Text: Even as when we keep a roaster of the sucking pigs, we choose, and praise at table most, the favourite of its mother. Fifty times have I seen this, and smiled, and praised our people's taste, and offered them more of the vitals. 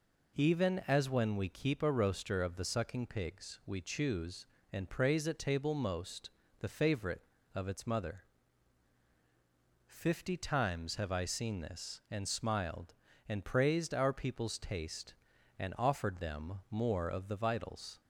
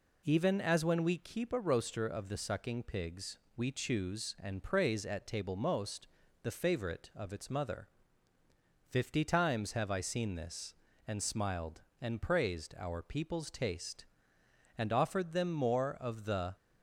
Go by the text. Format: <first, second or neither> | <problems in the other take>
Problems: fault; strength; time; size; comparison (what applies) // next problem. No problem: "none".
first | stops before "vitals"; at 16.5 s